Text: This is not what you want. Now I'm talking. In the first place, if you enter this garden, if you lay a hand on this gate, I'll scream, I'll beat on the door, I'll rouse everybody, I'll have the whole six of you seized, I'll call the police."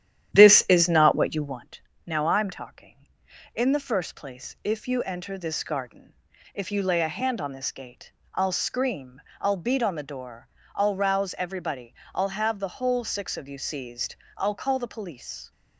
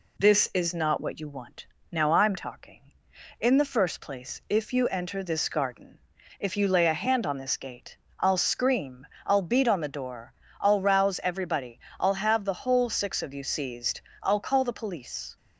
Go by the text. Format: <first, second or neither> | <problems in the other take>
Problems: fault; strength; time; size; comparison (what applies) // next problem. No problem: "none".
second | starts louder than the rest; strong; until 1.6 s; 10.5 dB